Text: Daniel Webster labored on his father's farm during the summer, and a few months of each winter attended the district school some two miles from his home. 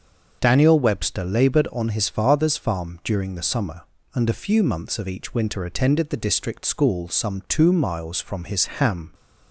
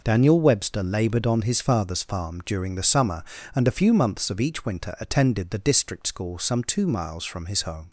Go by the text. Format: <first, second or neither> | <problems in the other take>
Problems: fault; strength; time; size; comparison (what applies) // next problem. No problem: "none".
second | starts louder than the rest; until 1.4 s; 6.5 dB // says "ham" for "home"; at 8.6 s